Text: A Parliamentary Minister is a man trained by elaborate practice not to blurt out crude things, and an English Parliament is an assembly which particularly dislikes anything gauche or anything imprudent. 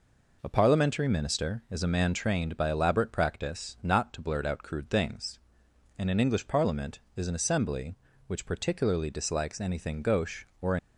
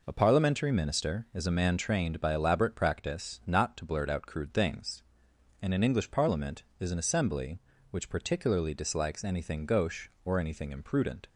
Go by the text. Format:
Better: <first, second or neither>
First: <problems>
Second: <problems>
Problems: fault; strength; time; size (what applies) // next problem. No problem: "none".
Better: second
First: stops before "anything imprudent"; at 10.7 s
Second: none